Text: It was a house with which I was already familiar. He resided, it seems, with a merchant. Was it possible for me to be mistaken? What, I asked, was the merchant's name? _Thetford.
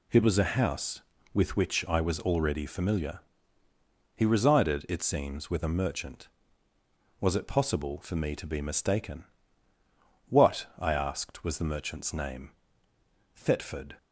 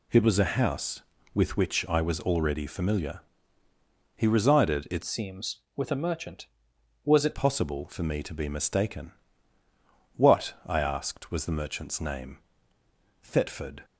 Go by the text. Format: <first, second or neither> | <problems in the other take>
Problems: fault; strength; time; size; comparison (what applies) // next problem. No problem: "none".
first | changes voice from "seems" to "it"; from 5.0 to 7.3 s; 2.3 s long